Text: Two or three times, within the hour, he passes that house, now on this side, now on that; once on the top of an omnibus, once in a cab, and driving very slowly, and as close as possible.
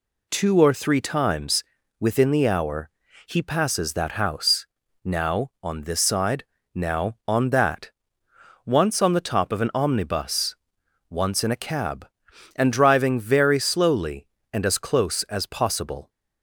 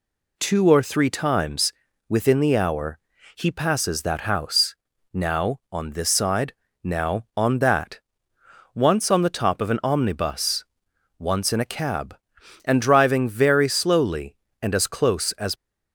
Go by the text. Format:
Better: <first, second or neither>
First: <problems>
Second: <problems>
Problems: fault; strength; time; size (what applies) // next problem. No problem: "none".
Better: first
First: none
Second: stops before "possible"; at 15.5 s